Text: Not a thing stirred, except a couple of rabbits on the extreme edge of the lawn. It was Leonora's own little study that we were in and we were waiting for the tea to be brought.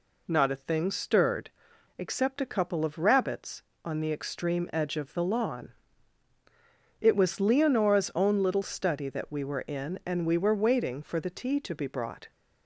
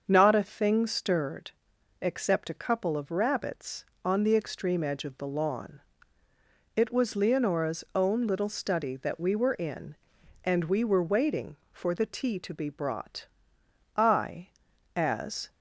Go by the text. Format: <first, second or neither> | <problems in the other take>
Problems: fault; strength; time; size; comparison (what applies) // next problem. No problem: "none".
first | starts louder than the rest; until 1.0 s; 7 dB // goes on to say "I as"; from 13.9 s on; 1.5 s long